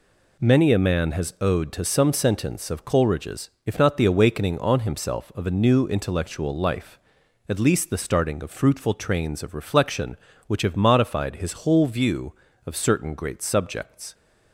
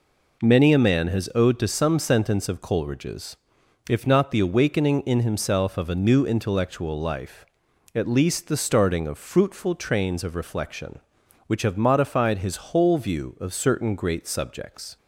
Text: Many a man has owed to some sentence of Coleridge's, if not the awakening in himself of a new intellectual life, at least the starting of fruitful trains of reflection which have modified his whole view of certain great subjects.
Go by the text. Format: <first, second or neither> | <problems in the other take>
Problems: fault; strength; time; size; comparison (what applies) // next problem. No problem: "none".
second | says "on" for "in"; at 4.5 s